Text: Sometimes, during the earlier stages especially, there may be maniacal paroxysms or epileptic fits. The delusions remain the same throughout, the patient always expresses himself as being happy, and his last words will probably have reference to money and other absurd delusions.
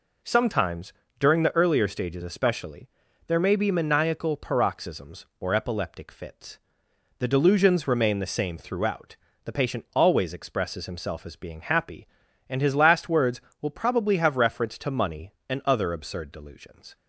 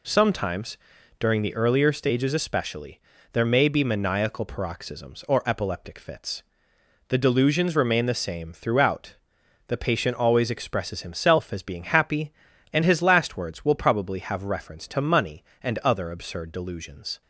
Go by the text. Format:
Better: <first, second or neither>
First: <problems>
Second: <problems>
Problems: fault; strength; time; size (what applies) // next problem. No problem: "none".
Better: neither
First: none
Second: none